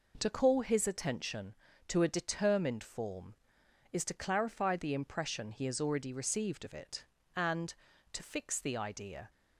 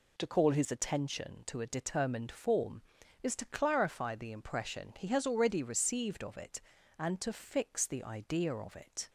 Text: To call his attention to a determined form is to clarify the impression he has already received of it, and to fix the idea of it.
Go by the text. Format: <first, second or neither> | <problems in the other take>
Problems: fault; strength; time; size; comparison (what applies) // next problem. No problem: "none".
second | stops before "of it"; at 9.2 s